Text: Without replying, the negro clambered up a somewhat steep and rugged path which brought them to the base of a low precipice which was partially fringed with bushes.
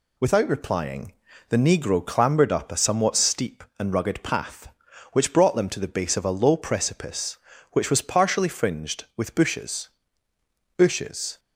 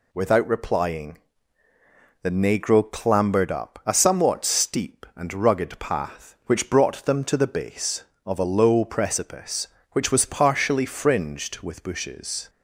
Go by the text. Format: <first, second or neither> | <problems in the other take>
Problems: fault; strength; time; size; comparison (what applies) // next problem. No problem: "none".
second | says "bushes" twice; at 10.7 s